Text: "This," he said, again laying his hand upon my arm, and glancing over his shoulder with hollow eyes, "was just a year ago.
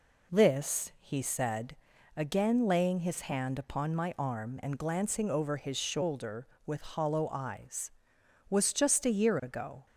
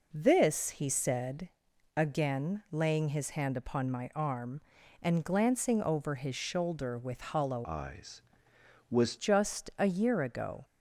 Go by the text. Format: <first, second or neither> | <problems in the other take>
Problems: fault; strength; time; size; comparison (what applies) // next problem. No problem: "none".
first | changes voice from "eyes" to "was"; from 7.6 to 9.1 s; 1.5 s long